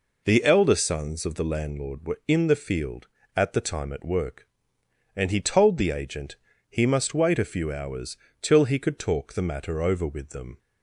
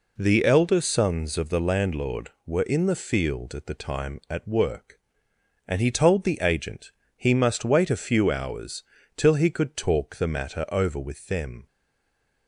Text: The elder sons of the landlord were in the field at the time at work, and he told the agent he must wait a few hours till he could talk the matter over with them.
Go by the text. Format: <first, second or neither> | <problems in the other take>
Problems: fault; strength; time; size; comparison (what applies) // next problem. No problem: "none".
first | pauses between "agent" and "he"; slight; at 6.9 s; 0.26 s long; slight in the first // pauses between "hours" and "till"; slight; at 8.8 s; 0.36 s long; slight in the first // stays silent after the last word; slight; from 11.6 s on; 0.8 s long